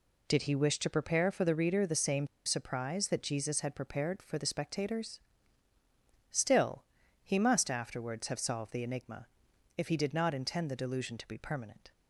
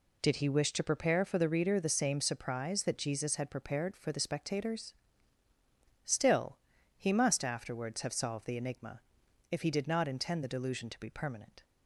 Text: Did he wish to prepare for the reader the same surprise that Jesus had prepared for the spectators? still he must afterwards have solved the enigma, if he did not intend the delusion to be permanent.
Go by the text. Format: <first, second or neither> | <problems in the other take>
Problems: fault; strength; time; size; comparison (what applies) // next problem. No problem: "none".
second | pauses between "same" and "surprise"; slight; at 2.2 s; 0.18 s long // pauses between "still" and "he"; at 6.8 s; 0.40 s long; also in the second